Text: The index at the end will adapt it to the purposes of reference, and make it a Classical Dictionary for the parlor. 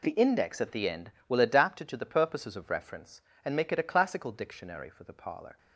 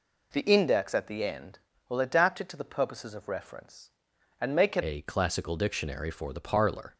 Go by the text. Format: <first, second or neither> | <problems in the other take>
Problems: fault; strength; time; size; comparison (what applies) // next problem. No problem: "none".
first | changes voice at "a"; from 4.8 s on; 2.1 s long